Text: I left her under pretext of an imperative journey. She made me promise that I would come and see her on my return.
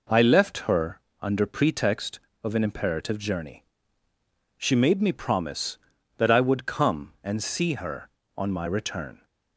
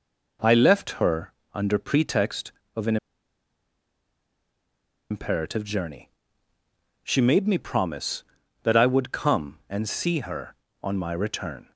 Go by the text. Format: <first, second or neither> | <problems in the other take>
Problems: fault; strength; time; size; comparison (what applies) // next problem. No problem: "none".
first | pauses between "her" and "under"; slight; at 1.3 s; 0.18 s long; slight in the first // pauses between "an" and "imperative"; strong; at 2.9 s; 2.1 s long